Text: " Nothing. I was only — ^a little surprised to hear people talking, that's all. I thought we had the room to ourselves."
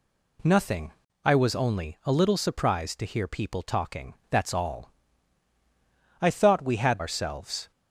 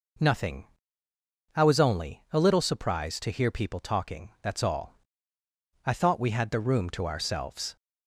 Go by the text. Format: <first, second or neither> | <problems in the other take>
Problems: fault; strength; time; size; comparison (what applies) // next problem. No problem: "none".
second | skips "the room to"; at 6.9 s